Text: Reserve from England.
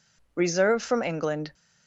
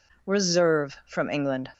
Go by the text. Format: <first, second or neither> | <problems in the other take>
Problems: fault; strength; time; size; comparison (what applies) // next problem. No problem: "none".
neither | none